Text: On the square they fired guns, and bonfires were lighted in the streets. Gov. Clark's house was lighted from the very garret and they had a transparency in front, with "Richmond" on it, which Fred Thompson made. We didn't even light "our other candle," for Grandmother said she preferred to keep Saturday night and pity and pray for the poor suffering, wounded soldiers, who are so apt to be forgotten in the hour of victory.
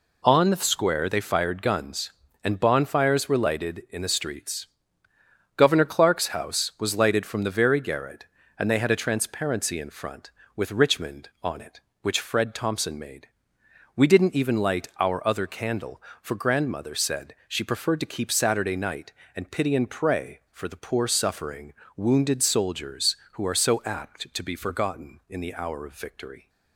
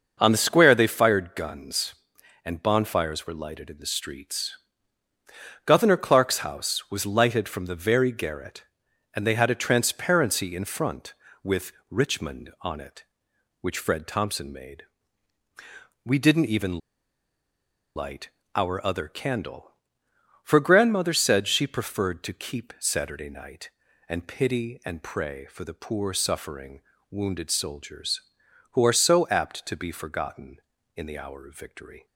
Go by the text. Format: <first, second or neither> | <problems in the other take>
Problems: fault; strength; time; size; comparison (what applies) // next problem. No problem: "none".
first | pauses between "with" and "Richmond"; slight; at 11.7 s; 0.16 s long // pauses between "even" and "light"; at 16.7 s; 1.1 s long // pauses between "light" and "our"; slight; at 18.3 s; 0.26 s long